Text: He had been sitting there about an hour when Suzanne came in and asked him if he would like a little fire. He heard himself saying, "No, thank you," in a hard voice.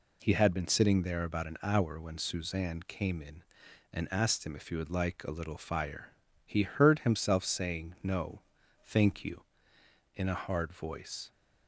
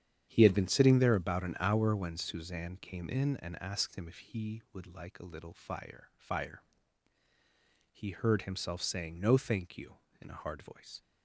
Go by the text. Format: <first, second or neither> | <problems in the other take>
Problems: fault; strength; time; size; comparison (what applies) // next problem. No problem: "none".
first | starts louder than the rest; strong; until 1.3 s; 9 dB // says "fire" twice; at 6.1 s